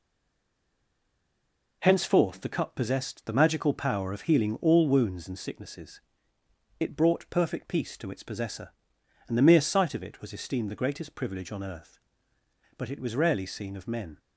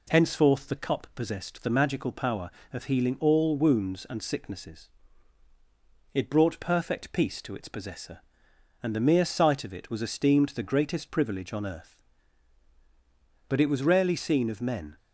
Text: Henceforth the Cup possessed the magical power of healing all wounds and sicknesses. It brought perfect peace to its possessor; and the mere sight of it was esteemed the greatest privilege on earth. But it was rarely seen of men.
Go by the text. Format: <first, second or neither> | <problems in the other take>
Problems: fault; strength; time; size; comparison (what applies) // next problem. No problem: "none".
second | stays silent before the first word; noticeable; until 1.8 s; 1.8 s long